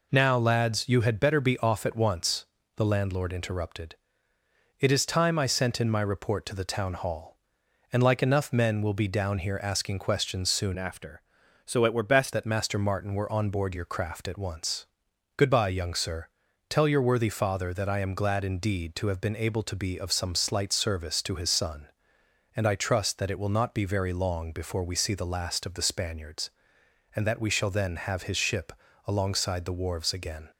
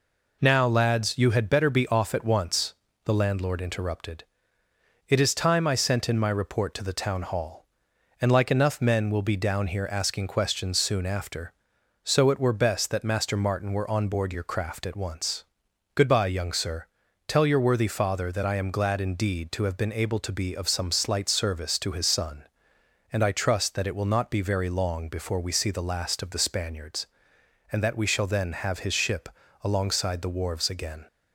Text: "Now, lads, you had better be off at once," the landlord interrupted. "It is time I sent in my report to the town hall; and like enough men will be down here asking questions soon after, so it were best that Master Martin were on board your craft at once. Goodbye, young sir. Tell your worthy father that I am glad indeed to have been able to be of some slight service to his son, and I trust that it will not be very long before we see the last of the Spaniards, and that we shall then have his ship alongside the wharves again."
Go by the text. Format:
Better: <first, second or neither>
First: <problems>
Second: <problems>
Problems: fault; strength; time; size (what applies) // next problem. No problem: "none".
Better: second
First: changes voice from "after" to "best"; from 10.7 to 12.3 s; 1.6 s long // pauses between "ship" and "alongside"; slight; at 28.7 s; 0.34 s long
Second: pauses between "ship" and "alongside"; slight; at 29.2 s; 0.34 s long